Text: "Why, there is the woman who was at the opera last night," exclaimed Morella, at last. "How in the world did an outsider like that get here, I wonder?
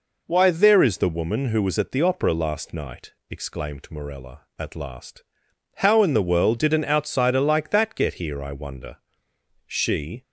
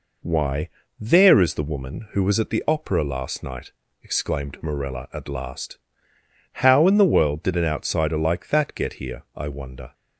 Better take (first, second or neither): second